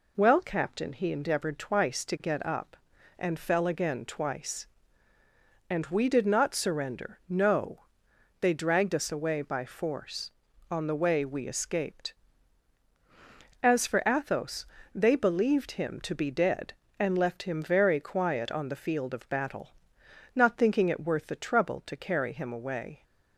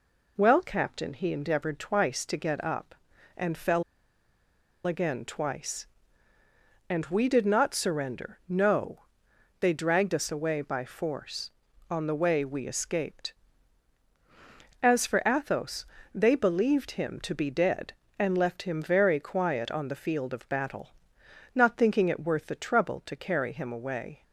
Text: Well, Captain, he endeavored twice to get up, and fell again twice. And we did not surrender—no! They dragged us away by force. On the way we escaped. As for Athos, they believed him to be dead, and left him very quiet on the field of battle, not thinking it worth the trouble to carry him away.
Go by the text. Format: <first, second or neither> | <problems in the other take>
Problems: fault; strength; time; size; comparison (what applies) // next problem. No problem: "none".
first | pauses between "fell" and "again"; at 3.8 s; 1.0 s long